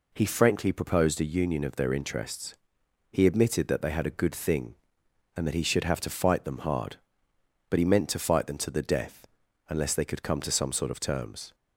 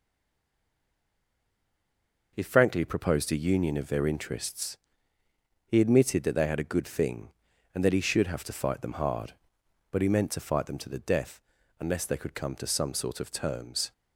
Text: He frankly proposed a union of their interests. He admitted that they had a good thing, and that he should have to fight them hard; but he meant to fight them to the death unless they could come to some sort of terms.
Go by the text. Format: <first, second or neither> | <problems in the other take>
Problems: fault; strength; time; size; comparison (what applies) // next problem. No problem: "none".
first | stays silent before the first word; until 2.3 s; 2.3 s long // pauses between "death" and "unless"; at 11.4 s; 0.38 s long; also in the first